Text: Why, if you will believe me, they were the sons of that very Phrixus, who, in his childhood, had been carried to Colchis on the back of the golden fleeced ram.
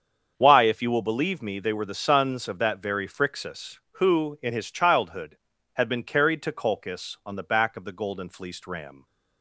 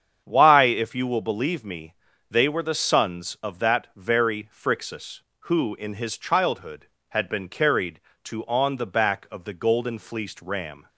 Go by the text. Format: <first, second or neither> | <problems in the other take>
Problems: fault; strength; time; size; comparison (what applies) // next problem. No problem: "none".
first | starts louder than the rest; strong; until 1.2 s; 7.5 dB; strong in the first // skips "Colchis"; at 8.4 s